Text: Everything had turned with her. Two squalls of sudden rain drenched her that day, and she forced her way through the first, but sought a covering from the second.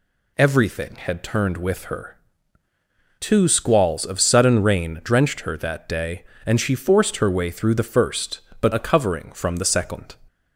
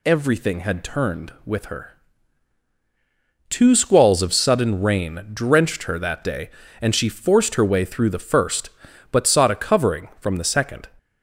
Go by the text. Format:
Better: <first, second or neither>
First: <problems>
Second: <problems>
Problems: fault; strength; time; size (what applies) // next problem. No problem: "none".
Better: second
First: skips "sought"; at 8.7 s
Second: none